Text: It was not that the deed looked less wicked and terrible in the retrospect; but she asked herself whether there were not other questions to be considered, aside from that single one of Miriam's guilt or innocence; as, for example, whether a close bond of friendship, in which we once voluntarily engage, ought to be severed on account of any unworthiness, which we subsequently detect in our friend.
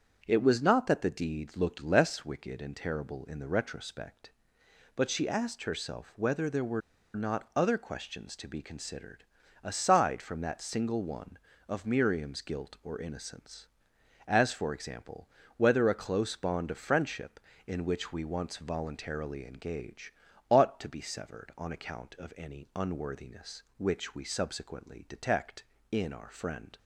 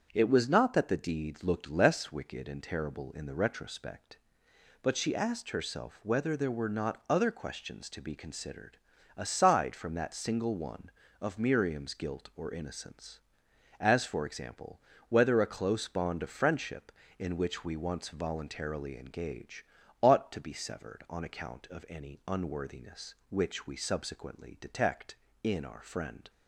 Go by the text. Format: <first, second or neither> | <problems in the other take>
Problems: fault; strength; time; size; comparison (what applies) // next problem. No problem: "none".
second | starts louder than the rest; strong; until 1.2 s; 7.5 dB; strong in the second // pauses between "were" and "not"; slight; at 6.8 s; 0.35 s long